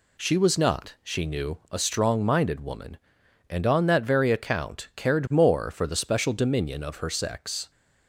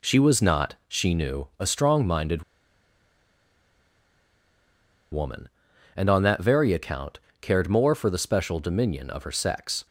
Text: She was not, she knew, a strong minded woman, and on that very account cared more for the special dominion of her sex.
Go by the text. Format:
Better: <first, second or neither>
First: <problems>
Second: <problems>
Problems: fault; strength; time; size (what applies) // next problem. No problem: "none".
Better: first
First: none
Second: pauses between "minded" and "woman"; strong; at 2.4 s; 2.7 s long // pauses between "account" and "cared"; slight; at 7.1 s; 0.24 s long